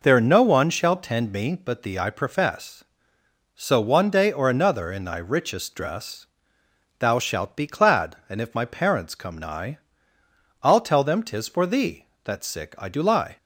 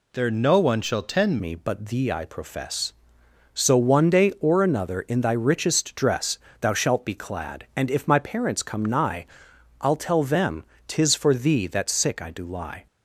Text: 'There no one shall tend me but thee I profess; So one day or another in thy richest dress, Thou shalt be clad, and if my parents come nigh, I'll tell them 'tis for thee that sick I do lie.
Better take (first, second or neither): first